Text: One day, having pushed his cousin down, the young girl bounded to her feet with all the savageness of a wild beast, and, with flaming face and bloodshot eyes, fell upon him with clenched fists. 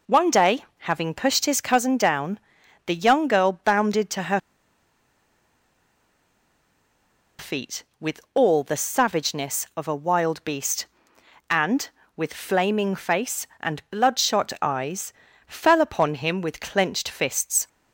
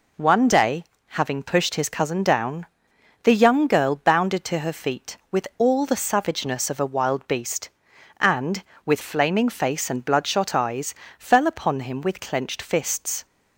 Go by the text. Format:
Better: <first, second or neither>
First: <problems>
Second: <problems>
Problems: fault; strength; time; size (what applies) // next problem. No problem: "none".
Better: second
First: pauses between "her" and "feet"; strong; at 4.3 s; 2.9 s long // pauses between "with" and "all"; slight; at 8.1 s; 0.16 s long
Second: none